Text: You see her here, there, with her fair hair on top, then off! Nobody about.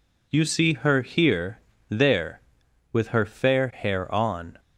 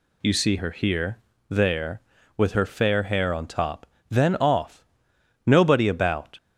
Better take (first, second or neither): second